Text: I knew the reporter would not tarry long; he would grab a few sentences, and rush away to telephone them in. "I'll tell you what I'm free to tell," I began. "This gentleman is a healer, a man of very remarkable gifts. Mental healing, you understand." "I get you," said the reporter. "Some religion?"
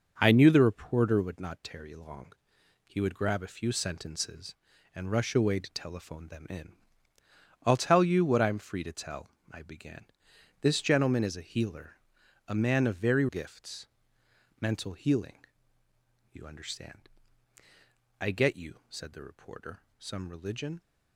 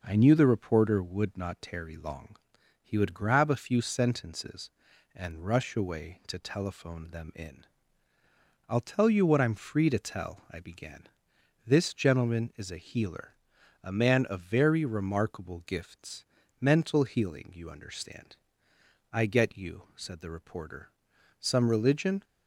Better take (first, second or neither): second